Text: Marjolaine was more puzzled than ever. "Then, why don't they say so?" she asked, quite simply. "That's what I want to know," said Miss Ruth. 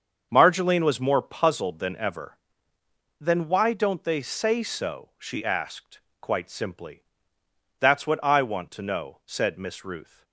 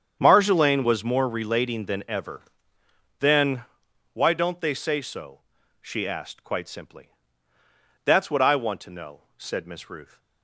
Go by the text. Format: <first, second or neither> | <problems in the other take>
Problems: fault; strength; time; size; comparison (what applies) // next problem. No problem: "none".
first | starts louder than the rest; strong; until 1.2 s; 8 dB; also in the first // says "relating" for "puzzled"; at 1.2 s